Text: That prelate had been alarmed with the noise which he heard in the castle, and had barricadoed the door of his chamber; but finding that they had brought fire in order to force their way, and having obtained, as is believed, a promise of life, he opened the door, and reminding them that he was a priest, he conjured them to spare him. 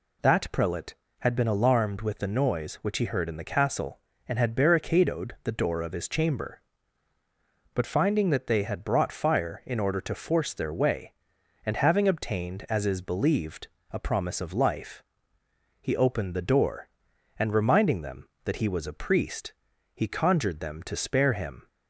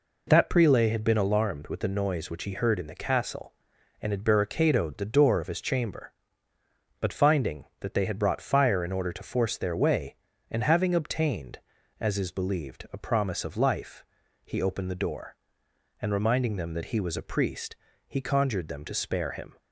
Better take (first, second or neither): neither